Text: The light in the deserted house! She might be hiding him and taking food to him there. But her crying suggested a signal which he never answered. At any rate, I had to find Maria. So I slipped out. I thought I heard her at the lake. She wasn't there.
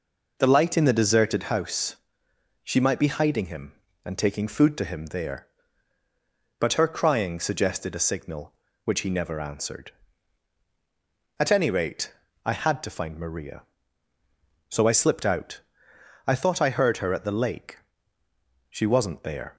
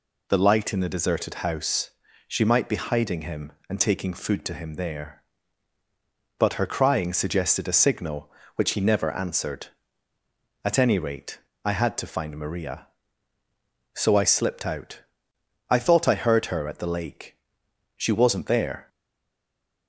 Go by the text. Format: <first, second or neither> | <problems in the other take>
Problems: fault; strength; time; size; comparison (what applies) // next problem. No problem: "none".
first | stays silent after the last word; from 18.8 s on; 1.0 s long